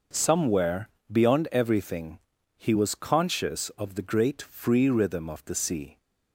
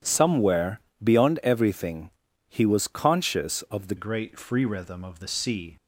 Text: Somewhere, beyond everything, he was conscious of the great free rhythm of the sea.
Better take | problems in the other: first | changes voice at "great"; from 3.9 s on; 1.8 s long

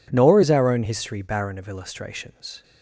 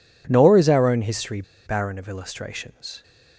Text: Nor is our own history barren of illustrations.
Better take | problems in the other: first | pauses between "history" and "barren"; slight; at 1.4 s; 0.24 s long

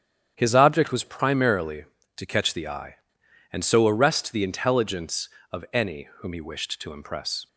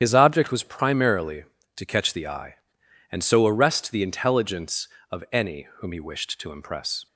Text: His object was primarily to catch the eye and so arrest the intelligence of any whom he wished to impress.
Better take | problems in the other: first | loses the start of "His"; at 0.0 s; 45 ms // starts louder than the rest; strong; until 1.0 s; 9 dB; strong in the first

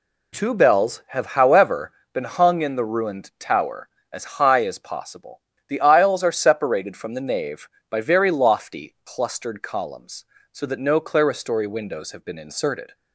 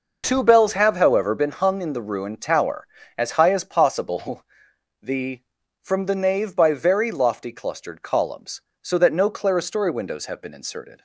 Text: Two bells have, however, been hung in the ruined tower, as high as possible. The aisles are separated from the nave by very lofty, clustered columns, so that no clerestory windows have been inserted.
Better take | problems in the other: first | skips "aisles are separated"; at 5.6 s

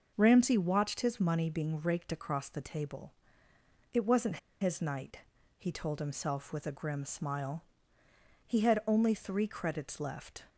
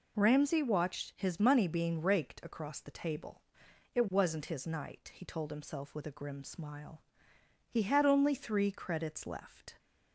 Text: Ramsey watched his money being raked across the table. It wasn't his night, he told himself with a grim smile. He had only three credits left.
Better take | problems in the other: second | pauses between "wasn't" and "his"; slight; at 4.3 s; 0.24 s long

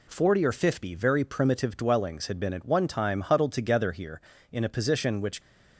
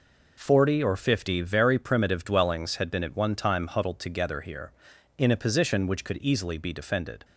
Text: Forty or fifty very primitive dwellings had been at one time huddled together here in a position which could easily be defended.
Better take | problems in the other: second | stops before "could easily be defended"; at 5.4 s

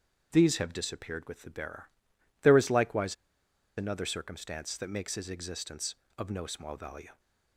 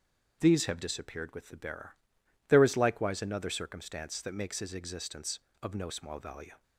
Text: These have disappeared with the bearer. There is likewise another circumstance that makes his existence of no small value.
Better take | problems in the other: second | starts louder than the rest; strong; until 1.3 s; 7.5 dB; strong in the second // pauses between "likewise" and "another"; noticeable; at 3.1 s; 0.62 s long

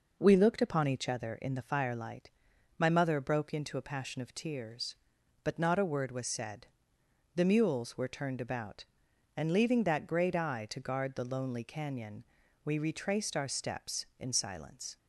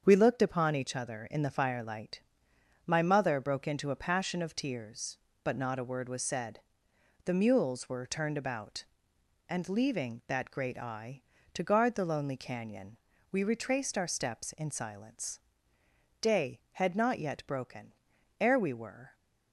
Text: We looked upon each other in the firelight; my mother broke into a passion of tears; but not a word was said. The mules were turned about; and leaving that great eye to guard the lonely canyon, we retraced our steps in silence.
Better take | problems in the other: first | starts louder than the rest; strong; until 1.0 s; 7 dB // goes on to say "Day had not yet broken ere we were"; strong; from 16.2 s on; 2.9 s long

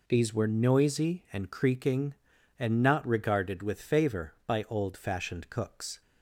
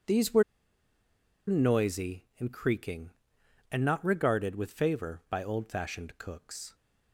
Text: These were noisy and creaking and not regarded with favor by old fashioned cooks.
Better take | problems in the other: first | pauses between "were" and "noisy"; at 0.4 s; 1.0 s long

